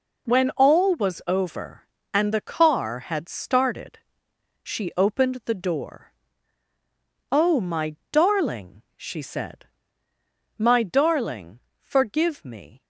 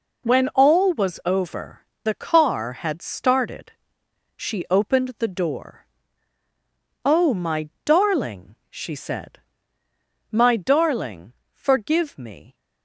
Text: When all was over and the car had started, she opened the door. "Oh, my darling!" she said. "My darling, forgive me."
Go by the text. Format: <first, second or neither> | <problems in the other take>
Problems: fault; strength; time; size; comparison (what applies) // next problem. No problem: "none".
first | skips "and"; at 1.9 s // pauses between "my" and "darling"; slight; at 7.6 s; 0.16 s long; slight in the first